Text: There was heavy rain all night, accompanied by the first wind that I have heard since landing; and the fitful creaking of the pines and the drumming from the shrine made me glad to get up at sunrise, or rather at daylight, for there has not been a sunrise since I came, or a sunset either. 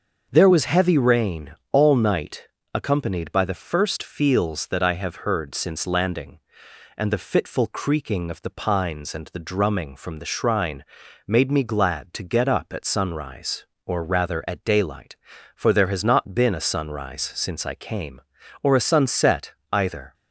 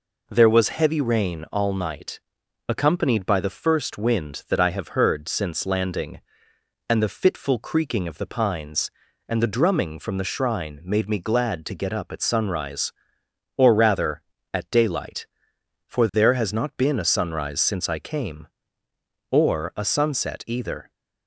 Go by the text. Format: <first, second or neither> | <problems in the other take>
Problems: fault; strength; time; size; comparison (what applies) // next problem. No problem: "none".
second | starts louder than the rest; noticeable; until 1.3 s; 6 dB // pauses between "rain" and "all"; slight; at 1.5 s; 0.16 s long // says "feels" for "wind"; at 4.0 s // pauses between "shrine" and "made"; noticeable; at 10.8 s; 0.46 s long // pauses between "sunset" and "either"; slight; at 19.5 s; 0.18 s long